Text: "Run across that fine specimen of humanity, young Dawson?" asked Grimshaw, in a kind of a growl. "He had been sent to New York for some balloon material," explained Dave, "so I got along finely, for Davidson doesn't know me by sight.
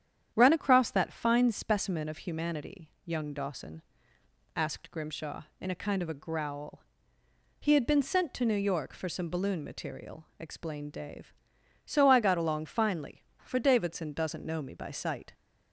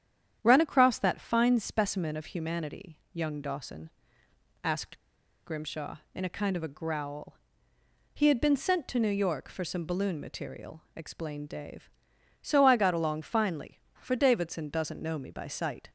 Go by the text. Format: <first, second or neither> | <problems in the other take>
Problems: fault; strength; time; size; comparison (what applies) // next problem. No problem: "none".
first | starts louder than the rest; strong; until 1.4 s; 9.5 dB; strong in the first // pauses between "asked" and "Grimshaw"; noticeable; at 4.9 s; 0.46 s long